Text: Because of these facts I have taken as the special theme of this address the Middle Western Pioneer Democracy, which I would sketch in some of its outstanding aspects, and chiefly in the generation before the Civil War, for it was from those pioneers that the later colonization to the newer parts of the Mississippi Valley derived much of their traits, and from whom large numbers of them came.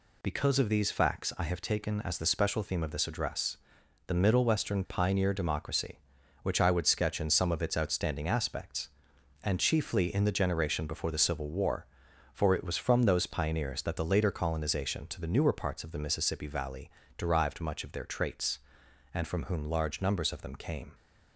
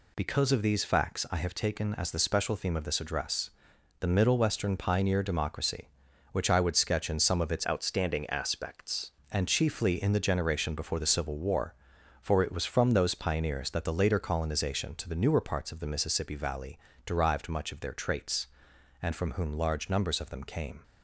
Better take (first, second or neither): first